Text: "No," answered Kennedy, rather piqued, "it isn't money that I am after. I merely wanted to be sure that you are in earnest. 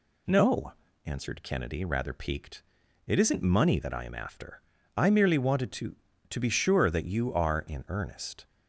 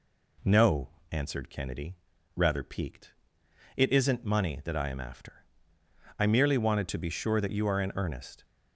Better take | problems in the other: second | says "to" twice; at 6.3 s

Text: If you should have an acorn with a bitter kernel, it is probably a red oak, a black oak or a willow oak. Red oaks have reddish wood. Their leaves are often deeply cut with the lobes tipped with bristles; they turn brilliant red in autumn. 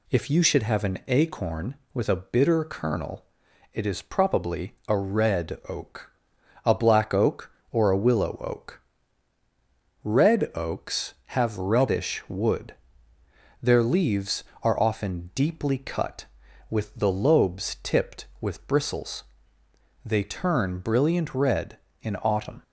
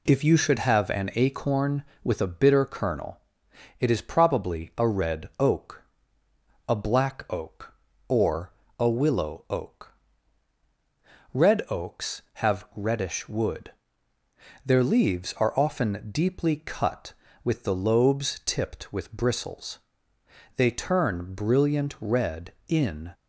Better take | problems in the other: first | pauses between "or" and "a"; slight; at 8.5 s; 0.26 s long // stops before "autumn"; at 23.1 s

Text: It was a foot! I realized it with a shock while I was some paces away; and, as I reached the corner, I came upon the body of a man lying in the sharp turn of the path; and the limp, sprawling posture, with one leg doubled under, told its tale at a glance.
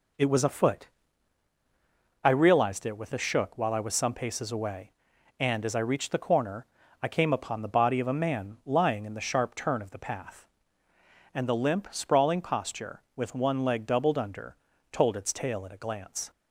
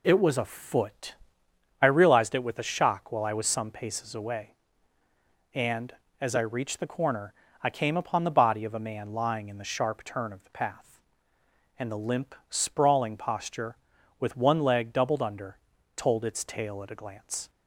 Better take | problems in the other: second | says "shook" for "shock"; at 3.1 s

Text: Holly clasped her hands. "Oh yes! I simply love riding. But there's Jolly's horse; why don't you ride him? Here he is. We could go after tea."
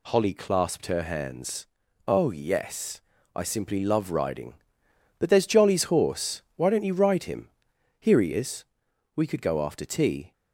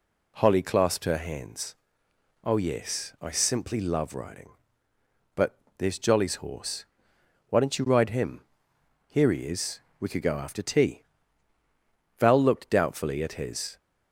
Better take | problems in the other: first | pauses between "But" and "there's"; slight; at 5.5 s; 0.18 s long // goes on to say "Val looked doubtfully at his"; from 12.1 s on; 1.6 s long

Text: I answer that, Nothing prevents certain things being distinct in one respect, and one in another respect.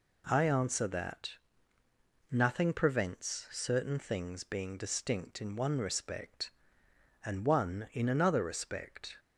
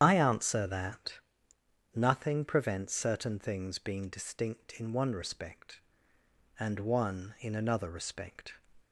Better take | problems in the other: first | loses the start of "I"; at 0.0 s; 45 ms // starts louder than the rest; strong; until 1.0 s; 9.5 dB

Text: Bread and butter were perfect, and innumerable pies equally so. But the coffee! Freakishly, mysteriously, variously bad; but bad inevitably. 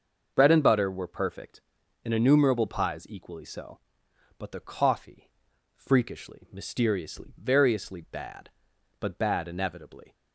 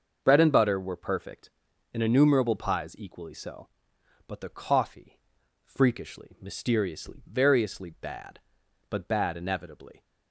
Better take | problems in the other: neither | starts louder than the rest; the same in both

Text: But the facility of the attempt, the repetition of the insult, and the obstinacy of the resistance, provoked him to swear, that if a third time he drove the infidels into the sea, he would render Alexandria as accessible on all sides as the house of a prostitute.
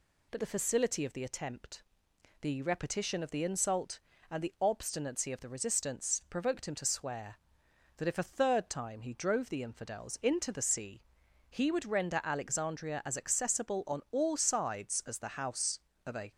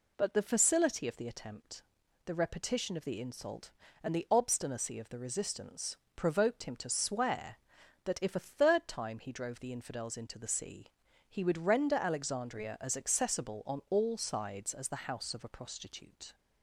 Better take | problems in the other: second | stops before "prostitute"; at 16.3 s

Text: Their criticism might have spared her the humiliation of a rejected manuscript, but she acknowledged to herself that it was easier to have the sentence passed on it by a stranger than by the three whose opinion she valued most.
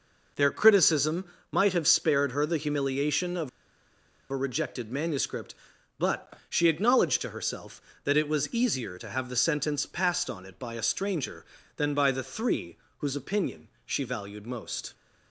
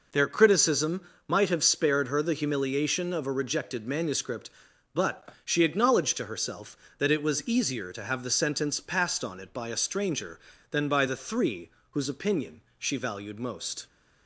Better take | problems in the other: second | pauses between "criticism" and "might"; slight; at 1.2 s; 0.24 s long; slight in the second // pauses between "of" and "a"; noticeable; at 3.4 s; 0.81 s long // pauses between "but" and "she"; slight; at 6.3 s; 0.16 s long; slight in the second // pauses between "three" and "whose"; slight; at 12.7 s; 0.20 s long; slight in the second // pauses between "opinion" and "she"; slight; at 13.6 s; 0.18 s long; slight in the second

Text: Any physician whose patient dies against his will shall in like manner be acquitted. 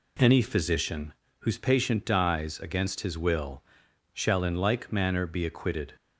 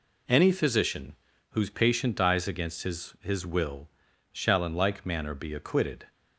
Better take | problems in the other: first | pauses between "physician" and "whose"; slight; at 1.1 s; 0.34 s long; slight in the first // says "his" twice; at 3.2 s // pauses between "will" and "shall"; at 3.8 s; 0.42 s long; noticeable in the first

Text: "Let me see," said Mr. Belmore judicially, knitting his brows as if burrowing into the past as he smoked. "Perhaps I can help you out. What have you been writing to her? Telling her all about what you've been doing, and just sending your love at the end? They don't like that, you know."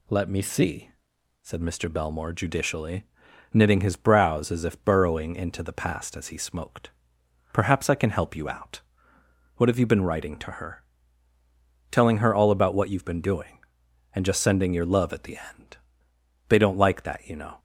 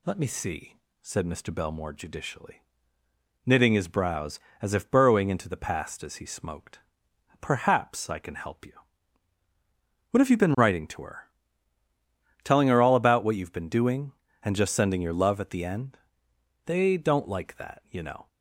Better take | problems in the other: first | skips "out"; at 9.4 s

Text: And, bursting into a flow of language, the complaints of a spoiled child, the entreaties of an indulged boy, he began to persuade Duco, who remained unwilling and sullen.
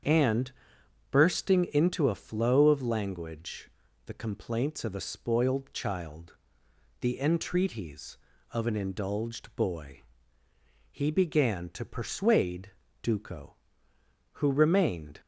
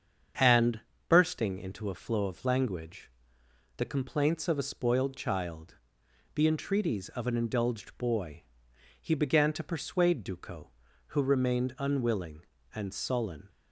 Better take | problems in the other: second | starts louder than the rest; strong; until 1.6 s; 8 dB; strong in the second // pauses between "persuade" and "Duco"; slight; at 12.6 s; 0.32 s long // stops before "unwilling and sullen"; at 15.1 s

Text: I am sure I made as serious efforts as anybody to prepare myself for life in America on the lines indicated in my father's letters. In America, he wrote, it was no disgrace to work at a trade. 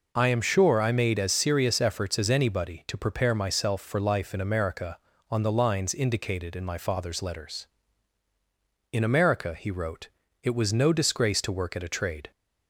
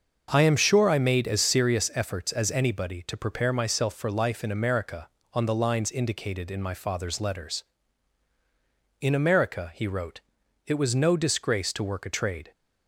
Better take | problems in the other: first | starts louder than the rest; until 1.3 s; 6.5 dB // skips "at"; at 12.0 s

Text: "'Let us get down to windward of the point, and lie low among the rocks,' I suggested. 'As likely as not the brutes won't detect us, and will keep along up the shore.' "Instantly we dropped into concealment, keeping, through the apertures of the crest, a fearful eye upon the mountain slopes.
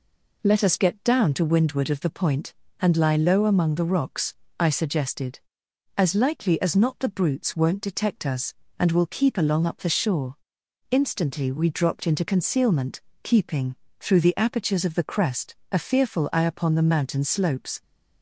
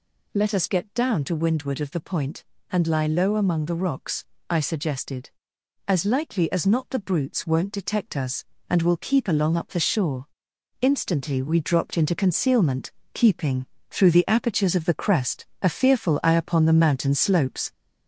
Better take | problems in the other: first | gets louder; throughout; 3.5 dB

